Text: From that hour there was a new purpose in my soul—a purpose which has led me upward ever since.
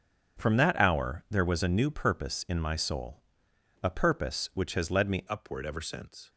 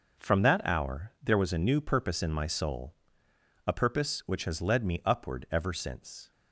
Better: second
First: starts louder than the rest; strong; until 1.4 s; 7.5 dB // changes voice at "upward"; from 5.2 s on; 1.0 s long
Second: none

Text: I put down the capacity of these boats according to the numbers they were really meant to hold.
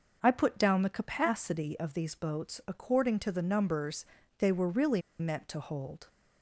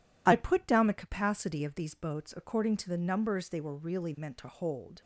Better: second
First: pauses between "numbers" and "they"; slight; at 4.0 s; 0.36 s long // pauses between "really" and "meant"; slight; at 5.0 s; 0.18 s long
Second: none

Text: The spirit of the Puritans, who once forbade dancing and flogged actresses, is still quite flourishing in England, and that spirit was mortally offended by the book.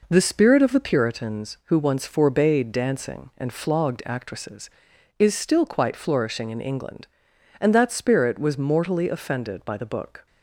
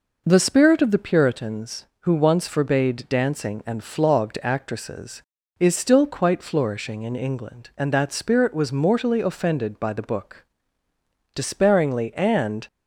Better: first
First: none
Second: goes on to say "Despairingly and"; from 11.3 s on; 1.3 s long

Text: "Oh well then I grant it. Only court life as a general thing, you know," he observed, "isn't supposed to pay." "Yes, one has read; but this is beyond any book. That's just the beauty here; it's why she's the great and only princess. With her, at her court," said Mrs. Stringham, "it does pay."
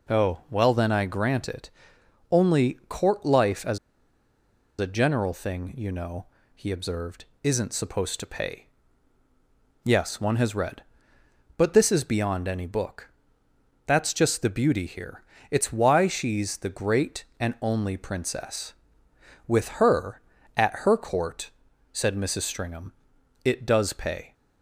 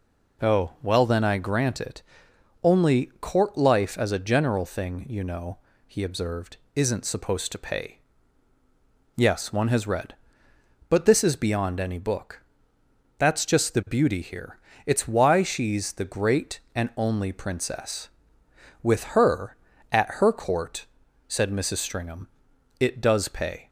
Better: second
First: pauses between "as" and "a"; at 3.7 s; 1.0 s long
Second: none

